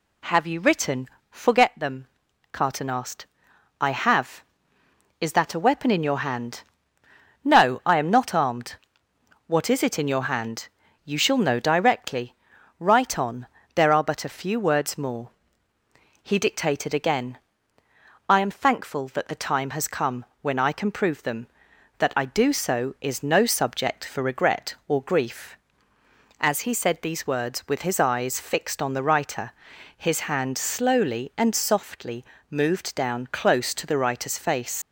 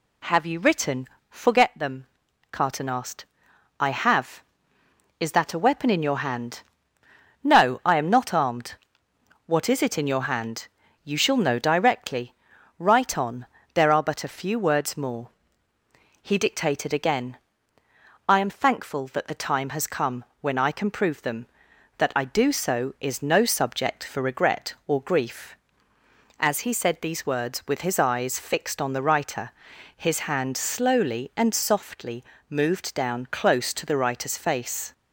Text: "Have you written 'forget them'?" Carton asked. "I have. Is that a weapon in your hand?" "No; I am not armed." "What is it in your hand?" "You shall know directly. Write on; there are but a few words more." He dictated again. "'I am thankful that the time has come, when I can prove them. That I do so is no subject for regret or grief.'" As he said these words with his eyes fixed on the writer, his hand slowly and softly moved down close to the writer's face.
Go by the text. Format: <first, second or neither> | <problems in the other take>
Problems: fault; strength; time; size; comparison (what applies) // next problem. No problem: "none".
second | pauses between "written" and "forget"; slight; at 1.0 s; 0.24 s long; slight in the second // pauses between "softly" and "moved"; slight; at 32.2 s; 0.26 s long; slight in the second // leaves "face" unfinished; at 34.8 s; 115 ms